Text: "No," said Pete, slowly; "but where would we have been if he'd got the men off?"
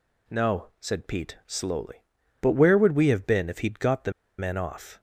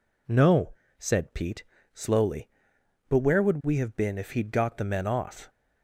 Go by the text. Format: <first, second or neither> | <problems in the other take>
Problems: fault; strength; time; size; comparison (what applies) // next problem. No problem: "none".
second | pauses between "the" and "men"; slight; at 4.1 s; 0.26 s long